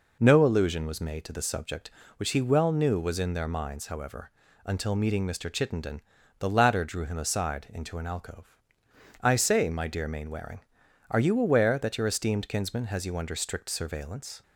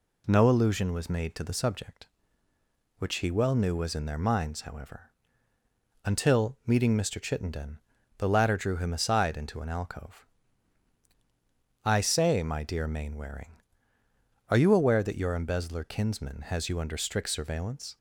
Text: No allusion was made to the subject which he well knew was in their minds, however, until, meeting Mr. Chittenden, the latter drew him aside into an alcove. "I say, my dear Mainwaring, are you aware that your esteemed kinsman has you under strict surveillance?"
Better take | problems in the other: first | says "embezzler" for "esteemed"; at 15.3 s

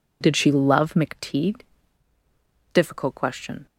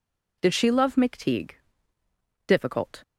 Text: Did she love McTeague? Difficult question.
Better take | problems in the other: first | stops before "question"; at 3.0 s

